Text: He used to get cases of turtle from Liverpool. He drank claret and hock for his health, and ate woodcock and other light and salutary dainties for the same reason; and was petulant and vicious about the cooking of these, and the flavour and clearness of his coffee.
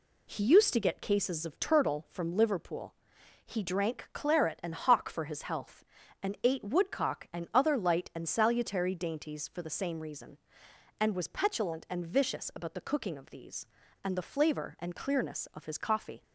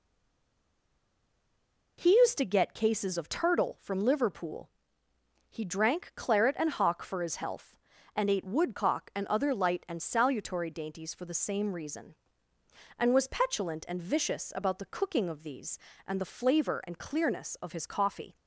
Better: first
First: none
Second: stays silent before the first word; noticeable; until 1.9 s; 1.9 s long

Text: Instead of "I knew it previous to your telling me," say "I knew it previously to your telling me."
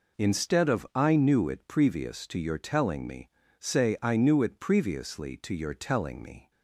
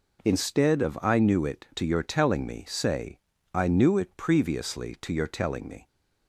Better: first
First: none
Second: skips "previous"; at 1.7 s // pauses between "say" and "I"; at 3.1 s; 0.38 s long

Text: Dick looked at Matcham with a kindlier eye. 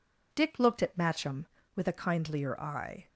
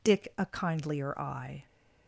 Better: first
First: none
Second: skips "looked at Matcham with"; at 0.3 s

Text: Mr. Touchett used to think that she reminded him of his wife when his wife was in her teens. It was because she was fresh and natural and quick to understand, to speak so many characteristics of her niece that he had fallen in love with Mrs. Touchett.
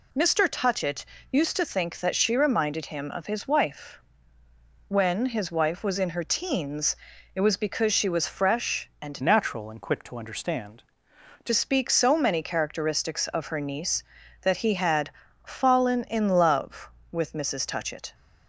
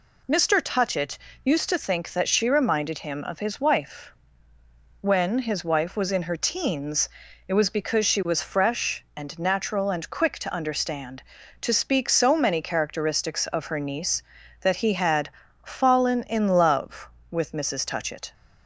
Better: second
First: pauses between "Touchett" and "used"; slight; at 1.0 s; 0.26 s long // pauses between "wife" and "when"; noticeable; at 4.0 s; 0.88 s long // changes voice from "natural" to "to"; from 9.2 to 11.5 s; 2.3 s long // pauses between "had" and "fallen"; slight; at 15.0 s; 0.34 s long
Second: pauses between "Touchett" and "used"; slight; at 1.1 s; 0.26 s long // pauses between "wife" and "when"; noticeable; at 4.1 s; 0.88 s long // pauses between "had" and "fallen"; slight; at 15.2 s; 0.34 s long

